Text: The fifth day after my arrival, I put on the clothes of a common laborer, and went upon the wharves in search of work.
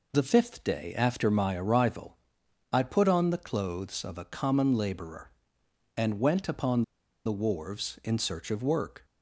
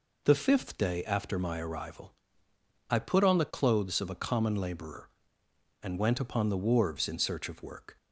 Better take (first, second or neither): second